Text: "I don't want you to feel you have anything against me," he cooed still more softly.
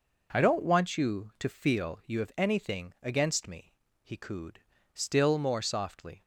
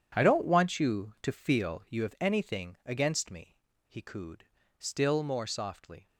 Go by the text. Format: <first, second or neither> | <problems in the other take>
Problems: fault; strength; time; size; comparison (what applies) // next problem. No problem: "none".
first | gets quieter; strong; throughout; 13 dB // pauses between "cooed" and "still"; slight; at 4.4 s; 0.34 s long; slight in the first